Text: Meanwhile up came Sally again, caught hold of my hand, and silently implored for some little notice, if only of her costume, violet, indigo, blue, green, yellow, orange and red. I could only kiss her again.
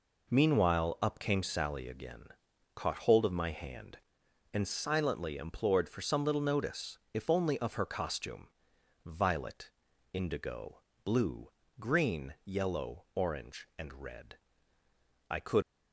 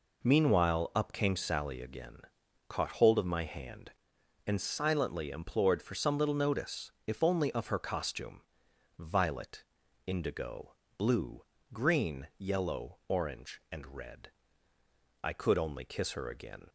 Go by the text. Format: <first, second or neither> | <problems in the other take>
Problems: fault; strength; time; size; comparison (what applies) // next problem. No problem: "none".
second | stops before "only kiss her again"; at 15.6 s